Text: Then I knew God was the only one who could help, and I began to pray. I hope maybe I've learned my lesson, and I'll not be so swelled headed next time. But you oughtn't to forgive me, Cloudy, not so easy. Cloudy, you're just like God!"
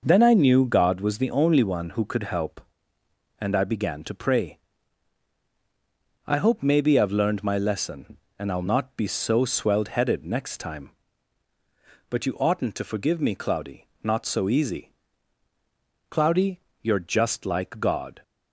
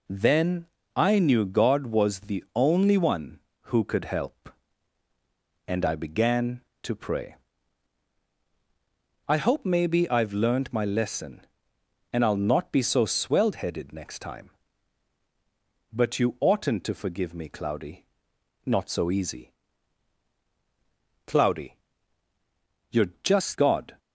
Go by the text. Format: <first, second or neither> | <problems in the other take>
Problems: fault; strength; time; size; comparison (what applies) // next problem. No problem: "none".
first | pauses between "Then" and "I"; slight; at 0.6 s; 0.28 s long // skips "like"; at 23.5 s